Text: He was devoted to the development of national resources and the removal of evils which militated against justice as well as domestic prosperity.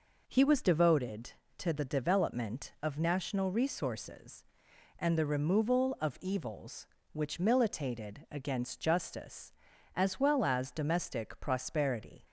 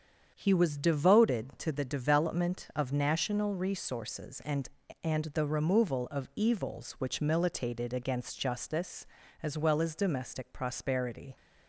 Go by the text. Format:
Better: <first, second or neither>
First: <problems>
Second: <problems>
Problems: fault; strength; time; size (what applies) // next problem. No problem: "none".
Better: first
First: none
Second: starts louder than the rest; strong; until 1.3 s; 7.5 dB // says "and" twice; at 5.0 s